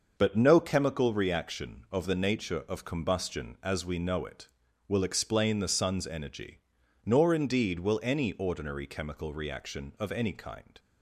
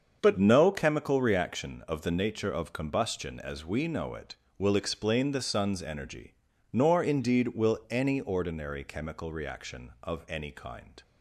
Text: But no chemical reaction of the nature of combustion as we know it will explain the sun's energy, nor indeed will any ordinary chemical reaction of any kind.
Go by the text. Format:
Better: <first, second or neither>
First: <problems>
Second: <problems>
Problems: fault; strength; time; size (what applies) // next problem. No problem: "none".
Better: neither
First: starts louder than the rest; noticeable; until 1.1 s; 6 dB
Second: starts louder than the rest; until 1.2 s; 7 dB